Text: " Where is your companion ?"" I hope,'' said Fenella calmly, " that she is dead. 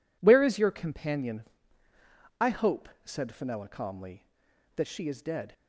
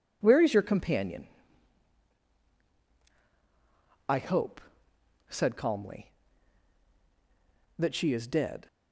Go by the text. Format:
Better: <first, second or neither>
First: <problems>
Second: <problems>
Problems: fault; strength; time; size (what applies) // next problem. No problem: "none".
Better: first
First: none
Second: starts louder than the rest; strong; until 1.2 s; 8.5 dB // skips "Fenella"; at 5.5 s